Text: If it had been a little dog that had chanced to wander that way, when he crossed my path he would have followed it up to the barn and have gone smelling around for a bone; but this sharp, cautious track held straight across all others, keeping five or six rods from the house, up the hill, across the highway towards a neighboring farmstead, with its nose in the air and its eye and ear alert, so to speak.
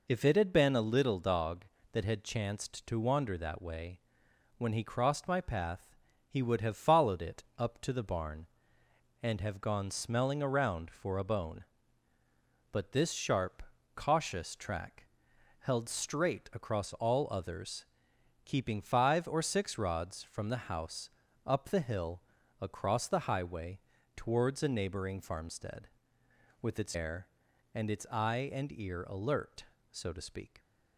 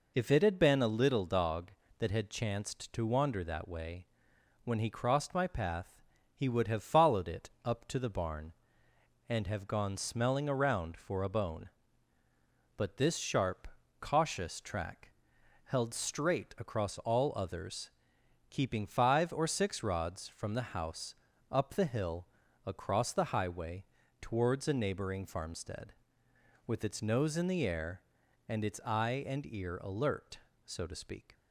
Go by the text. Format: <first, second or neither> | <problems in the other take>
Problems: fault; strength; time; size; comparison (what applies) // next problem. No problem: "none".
second | pauses between "path" and "he"; slight; at 5.9 s; 0.34 s long; slight in the second // pauses between "track" and "held"; noticeable; at 15.0 s; 0.54 s long; noticeable in the second // pauses between "highway" and "towards"; at 23.7 s; 0.38 s long; also in the second // skips "nose in the"; at 26.9 s